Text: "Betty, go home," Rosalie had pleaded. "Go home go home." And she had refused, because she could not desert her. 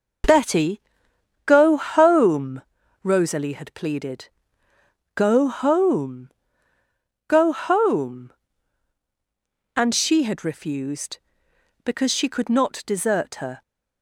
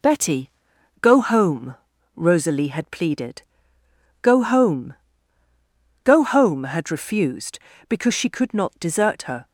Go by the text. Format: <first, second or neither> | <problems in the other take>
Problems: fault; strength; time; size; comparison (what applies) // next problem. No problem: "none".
first | pauses between "home" and "go"; at 4.9 s; 1.1 s long; noticeable in the first // skips "And she"; at 6.6 s